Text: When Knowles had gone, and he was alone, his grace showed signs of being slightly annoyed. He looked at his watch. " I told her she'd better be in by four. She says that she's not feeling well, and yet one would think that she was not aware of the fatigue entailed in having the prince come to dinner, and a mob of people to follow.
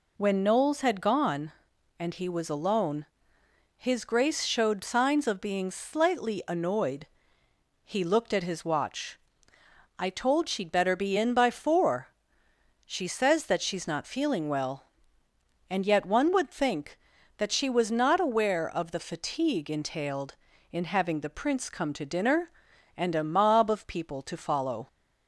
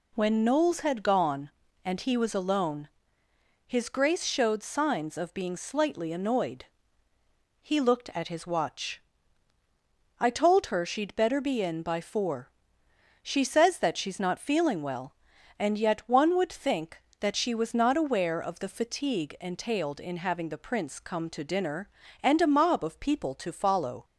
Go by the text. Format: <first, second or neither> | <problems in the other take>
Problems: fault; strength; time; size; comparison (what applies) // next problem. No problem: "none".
second | skips "her"; at 10.4 s